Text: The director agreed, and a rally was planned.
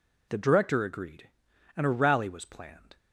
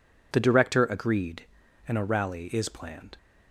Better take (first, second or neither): first